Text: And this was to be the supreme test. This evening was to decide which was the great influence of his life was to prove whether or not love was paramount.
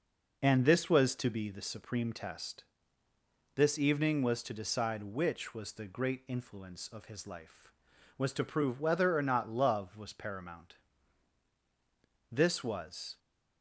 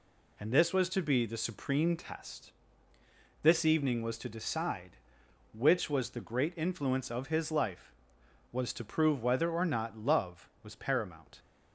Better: second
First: goes on to say "This was"; noticeable; from 12.3 s on; 0.86 s long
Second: none

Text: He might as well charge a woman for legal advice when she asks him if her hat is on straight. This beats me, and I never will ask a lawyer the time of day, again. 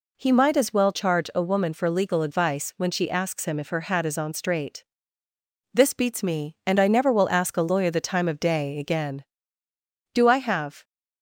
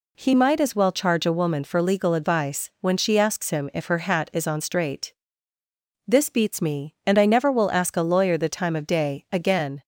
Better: second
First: goes on to say "Do I have"; noticeable; from 10.1 s on; 0.70 s long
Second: none

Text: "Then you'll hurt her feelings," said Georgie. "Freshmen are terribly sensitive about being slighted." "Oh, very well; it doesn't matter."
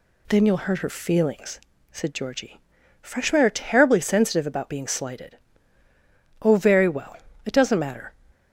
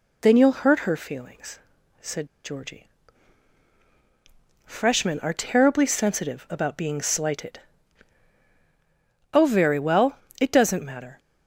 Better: first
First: none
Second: pauses between "said" and "Georgie"; slight; at 2.2 s; 0.18 s long

